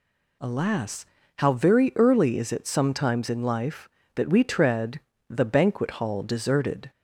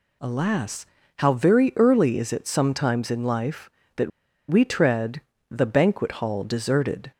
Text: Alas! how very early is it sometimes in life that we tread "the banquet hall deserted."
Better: first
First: pauses between "tread" and "the"; slight; at 4.9 s; 0.30 s long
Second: pauses between "that" and "we"; at 4.1 s; 0.40 s long // pauses between "tread" and "the"; slight; at 5.1 s; 0.30 s long

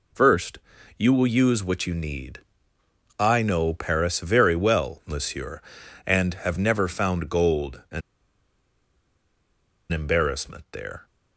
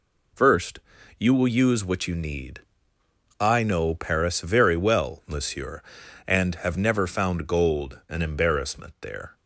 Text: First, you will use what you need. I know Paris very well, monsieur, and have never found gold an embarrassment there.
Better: second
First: pauses between "an" and "embarrassment"; strong; at 8.0 s; 1.9 s long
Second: none

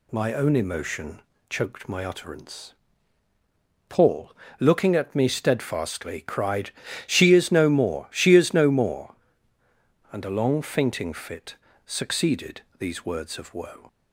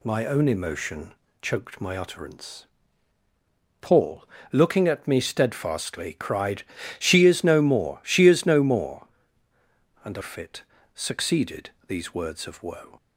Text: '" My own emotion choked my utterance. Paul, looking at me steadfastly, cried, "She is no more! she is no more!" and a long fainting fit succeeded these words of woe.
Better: first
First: pauses between "emotion" and "choked"; slight; at 1.1 s; 0.30 s long // pauses between "fit" and "succeeded"; slight; at 11.5 s; 0.30 s long // pauses between "succeeded" and "these"; slight; at 12.6 s; 0.16 s long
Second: pauses between "emotion" and "choked"; slight; at 1.1 s; 0.30 s long // skips "long fainting"; at 10.2 s // pauses between "fit" and "succeeded"; slight; at 10.6 s; 0.32 s long // pauses between "succeeded" and "these"; slight; at 11.7 s; 0.16 s long

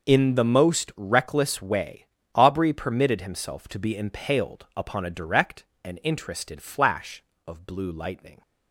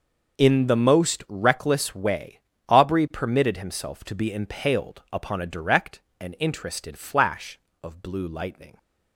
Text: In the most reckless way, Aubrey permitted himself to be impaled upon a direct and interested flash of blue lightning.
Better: neither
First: none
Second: none

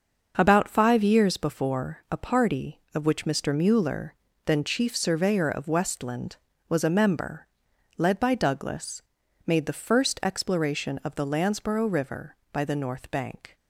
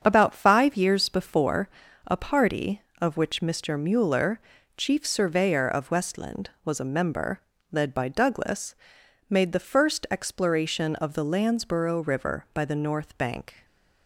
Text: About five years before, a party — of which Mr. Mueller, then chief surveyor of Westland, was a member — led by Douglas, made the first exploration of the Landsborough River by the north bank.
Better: first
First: starts louder than the rest; until 1.3 s; 6.5 dB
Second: starts louder than the rest; strong; until 1.0 s; 7.5 dB // skips "then"; at 4.5 s

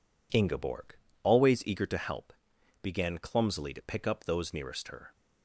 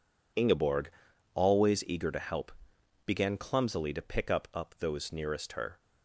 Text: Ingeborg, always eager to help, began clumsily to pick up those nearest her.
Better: first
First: none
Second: says "up" twice; at 4.5 s

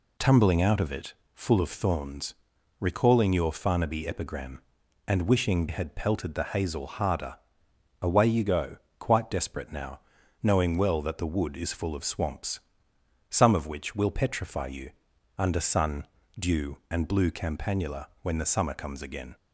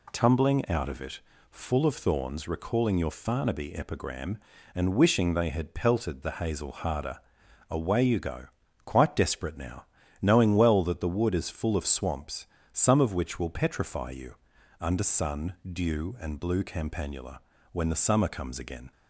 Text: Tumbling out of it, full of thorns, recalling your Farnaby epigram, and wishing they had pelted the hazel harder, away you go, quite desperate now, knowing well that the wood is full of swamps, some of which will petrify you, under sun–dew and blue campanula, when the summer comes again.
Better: second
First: skips "they"; at 5.6 s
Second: none

